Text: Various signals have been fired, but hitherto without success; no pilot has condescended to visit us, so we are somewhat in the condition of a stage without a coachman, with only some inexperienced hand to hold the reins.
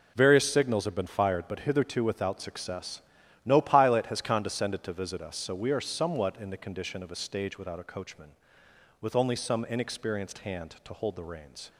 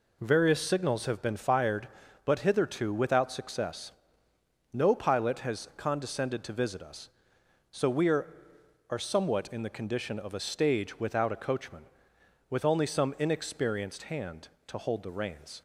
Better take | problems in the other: first | says "are" twice; at 8.8 s

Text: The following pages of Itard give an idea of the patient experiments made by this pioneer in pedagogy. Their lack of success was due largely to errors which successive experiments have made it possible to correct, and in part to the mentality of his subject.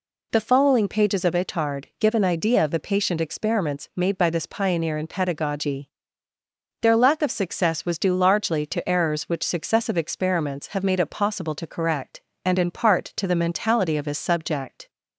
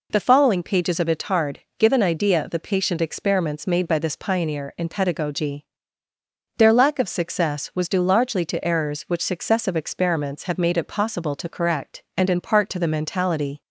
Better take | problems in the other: first | pauses between "Itard" and "give"; slight; at 1.5 s; 0.20 s long // stops before "of his subject"; at 13.6 s

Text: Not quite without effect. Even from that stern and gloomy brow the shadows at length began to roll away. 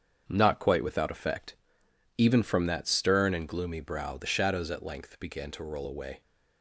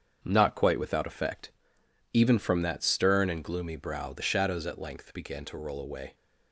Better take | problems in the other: neither | starts louder than the rest; strong; the same in both

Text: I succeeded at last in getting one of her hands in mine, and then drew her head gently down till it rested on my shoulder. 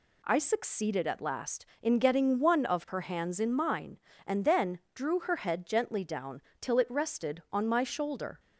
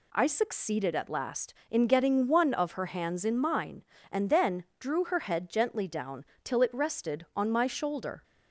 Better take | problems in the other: neither | pauses between "down" and "till"; slight; the same in both

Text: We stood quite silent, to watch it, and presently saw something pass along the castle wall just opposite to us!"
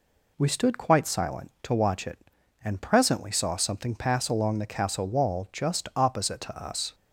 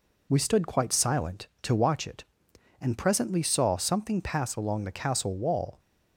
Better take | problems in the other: first | stops before "just opposite to us"; at 5.7 s

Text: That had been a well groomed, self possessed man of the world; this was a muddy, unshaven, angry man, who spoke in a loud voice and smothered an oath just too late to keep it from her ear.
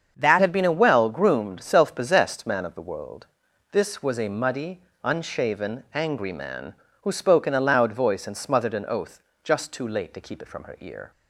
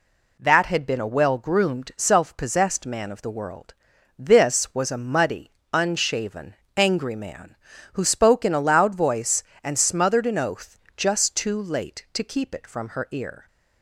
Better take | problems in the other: second | starts louder than the rest; until 1.1 s; 7 dB // changes voice at "had"; from 0.4 s on; 10.7 s long // pauses between "oath" and "just"; slight; at 9.2 s; 0.22 s long; slight in the second

